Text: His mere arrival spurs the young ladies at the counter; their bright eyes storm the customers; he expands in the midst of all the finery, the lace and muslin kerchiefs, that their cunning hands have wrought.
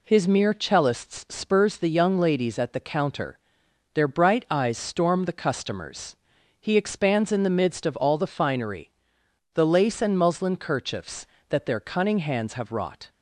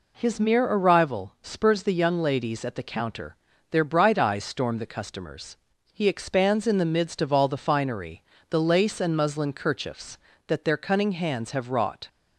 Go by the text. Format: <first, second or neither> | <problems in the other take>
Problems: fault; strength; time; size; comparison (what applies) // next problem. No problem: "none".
second | says "cellists" for "arrival"; at 0.5 s